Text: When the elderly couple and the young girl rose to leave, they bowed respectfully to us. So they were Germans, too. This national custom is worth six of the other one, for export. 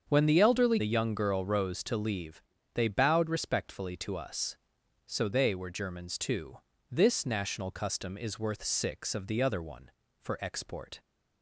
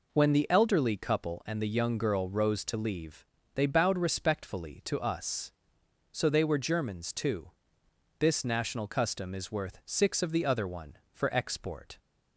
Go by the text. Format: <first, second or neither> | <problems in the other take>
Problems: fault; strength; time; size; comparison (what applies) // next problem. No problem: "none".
second | starts louder than the rest; strong; until 1.1 s; 7 dB // skips "couple and"; at 0.7 s